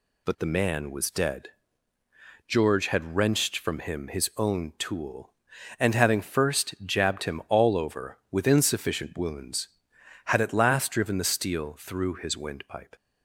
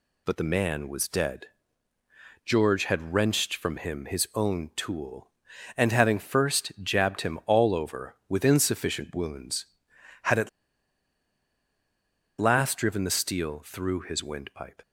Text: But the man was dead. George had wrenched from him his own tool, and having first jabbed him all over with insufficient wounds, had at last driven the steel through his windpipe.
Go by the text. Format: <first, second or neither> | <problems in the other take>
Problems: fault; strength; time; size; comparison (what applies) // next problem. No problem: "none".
first | pauses between "at" and "last"; strong; at 10.4 s; 1.9 s long